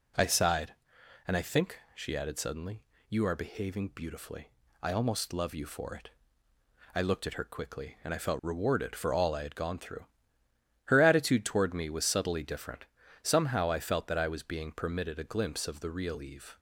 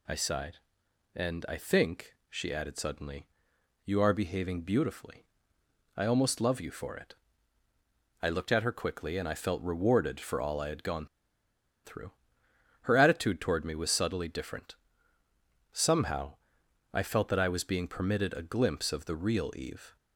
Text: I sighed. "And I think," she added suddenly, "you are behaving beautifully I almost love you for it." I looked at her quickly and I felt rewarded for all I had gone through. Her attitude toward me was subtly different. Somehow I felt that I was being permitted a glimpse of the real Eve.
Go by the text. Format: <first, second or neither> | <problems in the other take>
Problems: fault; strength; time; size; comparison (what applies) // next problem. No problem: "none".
first | pauses between "beautifully" and "I"; noticeable; at 5.2 s; 0.72 s long; slight in the first // pauses between "gone" and "through"; noticeable; at 11.0 s; 0.79 s long // pauses between "Somehow" and "I"; noticeable; at 16.3 s; 0.58 s long